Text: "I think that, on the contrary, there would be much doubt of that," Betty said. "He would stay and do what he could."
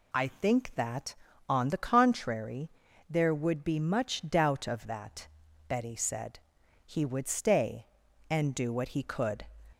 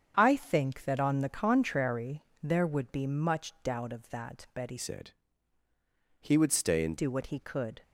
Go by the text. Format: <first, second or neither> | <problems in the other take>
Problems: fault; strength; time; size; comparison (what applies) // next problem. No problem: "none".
first | starts louder than the rest; strong; until 1.1 s; 7.5 dB // changes voice from "said" to "and"; from 4.7 to 6.9 s; 2.2 s long